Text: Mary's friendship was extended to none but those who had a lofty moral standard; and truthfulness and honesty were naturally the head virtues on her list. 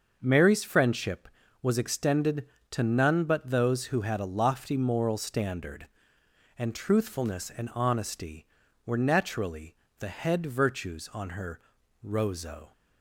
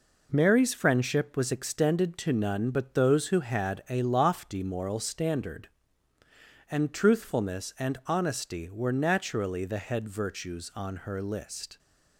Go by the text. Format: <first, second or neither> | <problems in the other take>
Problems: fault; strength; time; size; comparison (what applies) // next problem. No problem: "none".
second | starts louder than the rest; until 1.2 s; 6 dB // pauses between "naturally" and "the"; slight; at 9.7 s; 0.24 s long // says "rozo" for "list"; at 12.0 s